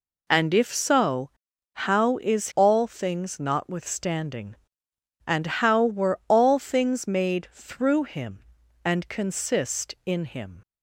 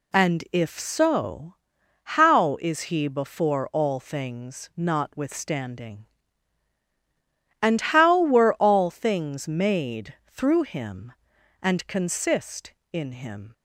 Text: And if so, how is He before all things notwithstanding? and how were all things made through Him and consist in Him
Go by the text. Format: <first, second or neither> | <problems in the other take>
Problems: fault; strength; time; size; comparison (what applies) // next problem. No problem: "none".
second | skips "He before"; at 2.5 s